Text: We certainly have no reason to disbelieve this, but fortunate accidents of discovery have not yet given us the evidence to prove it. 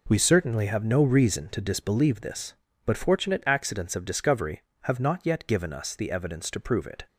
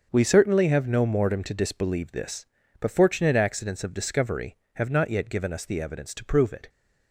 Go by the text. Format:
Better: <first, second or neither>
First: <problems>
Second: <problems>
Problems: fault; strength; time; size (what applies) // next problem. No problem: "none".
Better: first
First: none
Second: starts louder than the rest; until 1.1 s; 6.5 dB // says "mortem" for "reason"; at 1.0 s